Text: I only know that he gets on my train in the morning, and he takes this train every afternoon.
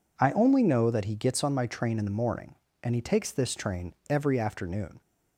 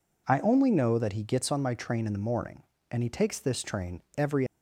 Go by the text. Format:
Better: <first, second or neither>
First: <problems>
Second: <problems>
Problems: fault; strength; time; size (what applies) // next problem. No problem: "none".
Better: first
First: pauses between "train" and "every"; slight; at 3.9 s; 0.16 s long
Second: pauses between "train" and "every"; slight; at 3.9 s; 0.16 s long // stops before "afternoon"; at 4.4 s